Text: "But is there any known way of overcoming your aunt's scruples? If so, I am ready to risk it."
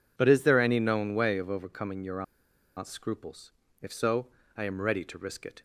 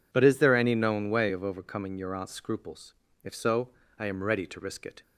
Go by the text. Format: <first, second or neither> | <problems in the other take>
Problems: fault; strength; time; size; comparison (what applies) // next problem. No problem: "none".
second | pauses between "your" and "aunt's"; noticeable; at 2.2 s; 0.54 s long